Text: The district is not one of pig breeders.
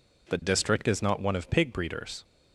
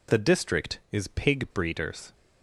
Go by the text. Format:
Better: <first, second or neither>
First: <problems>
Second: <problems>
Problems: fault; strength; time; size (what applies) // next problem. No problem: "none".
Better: first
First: none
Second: skips "not one of"; at 1.0 s